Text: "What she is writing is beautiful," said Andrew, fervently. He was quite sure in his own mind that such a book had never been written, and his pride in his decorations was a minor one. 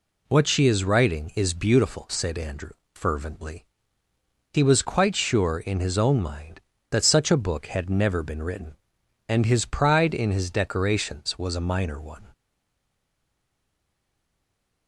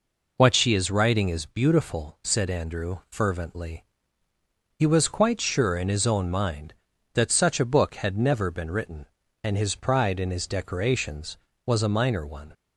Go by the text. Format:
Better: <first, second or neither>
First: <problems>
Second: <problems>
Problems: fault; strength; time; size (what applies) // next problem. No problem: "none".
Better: second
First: stays silent after the last word; strong; from 12.3 s on; 2.5 s long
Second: none